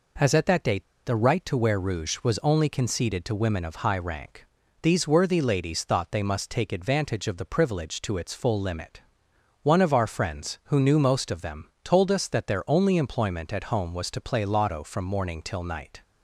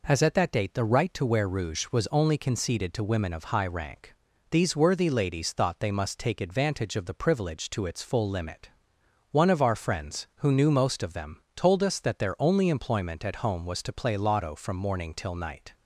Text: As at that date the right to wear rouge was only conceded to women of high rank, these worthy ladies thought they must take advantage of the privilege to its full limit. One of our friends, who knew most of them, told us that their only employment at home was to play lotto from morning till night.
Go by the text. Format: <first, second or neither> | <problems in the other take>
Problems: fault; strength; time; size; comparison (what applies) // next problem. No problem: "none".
second | pauses between "date" and "the"; slight; at 0.8 s; 0.21 s long